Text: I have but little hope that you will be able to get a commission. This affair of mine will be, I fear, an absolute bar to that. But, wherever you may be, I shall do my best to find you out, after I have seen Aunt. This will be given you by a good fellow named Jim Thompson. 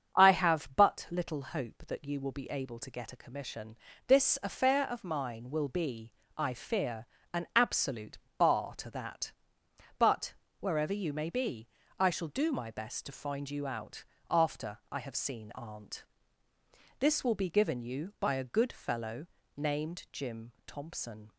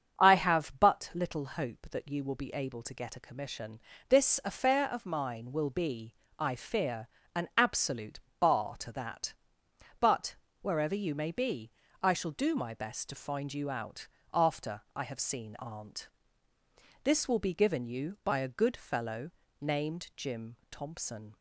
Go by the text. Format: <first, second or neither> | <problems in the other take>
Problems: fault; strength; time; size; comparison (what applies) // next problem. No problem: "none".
neither | starts louder than the rest; the same in both // pauses between "absolute" and "bar"; slight; the same in both // pauses between "fellow" and "named"; slight; the same in both